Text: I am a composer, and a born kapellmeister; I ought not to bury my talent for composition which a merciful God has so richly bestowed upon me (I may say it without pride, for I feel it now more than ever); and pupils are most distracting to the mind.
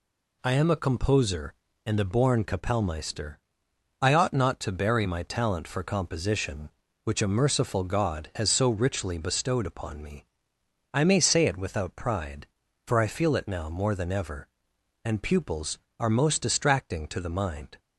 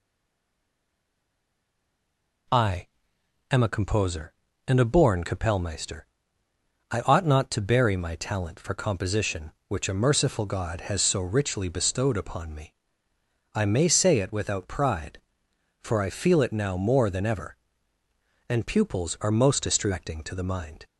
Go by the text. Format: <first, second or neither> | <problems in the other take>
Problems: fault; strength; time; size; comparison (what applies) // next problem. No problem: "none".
first | stays silent before the first word; until 2.4 s; 2.4 s long // pauses between "I" and "am"; noticeable; at 2.8 s; 0.66 s long